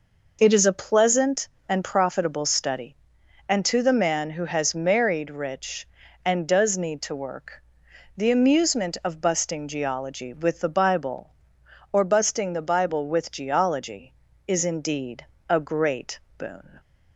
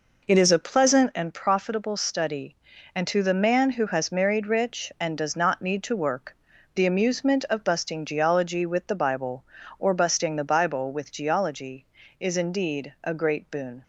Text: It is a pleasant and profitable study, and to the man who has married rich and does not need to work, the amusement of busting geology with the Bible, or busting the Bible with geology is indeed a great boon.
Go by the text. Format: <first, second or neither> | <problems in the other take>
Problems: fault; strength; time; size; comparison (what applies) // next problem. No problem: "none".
second | skips "not"; at 6.7 s // pauses between "indeed" and "a"; slight; at 15.2 s; 0.24 s long // pauses between "great" and "boon"; slight; at 16.1 s; 0.18 s long